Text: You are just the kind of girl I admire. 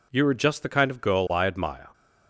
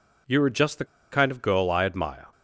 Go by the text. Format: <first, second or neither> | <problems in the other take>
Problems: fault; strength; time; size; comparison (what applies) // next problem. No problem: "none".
first | pauses between "the" and "kind"; slight; at 0.8 s; 0.27 s long